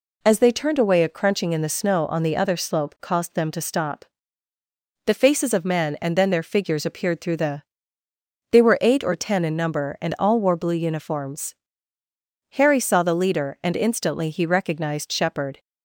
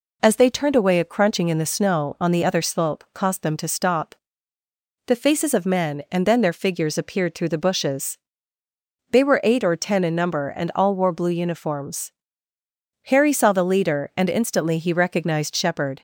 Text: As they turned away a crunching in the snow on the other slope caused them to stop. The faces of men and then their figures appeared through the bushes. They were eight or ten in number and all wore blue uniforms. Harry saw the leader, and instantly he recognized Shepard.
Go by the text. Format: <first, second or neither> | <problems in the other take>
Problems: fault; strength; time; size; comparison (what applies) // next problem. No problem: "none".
second | skips "bushes"; at 8.0 s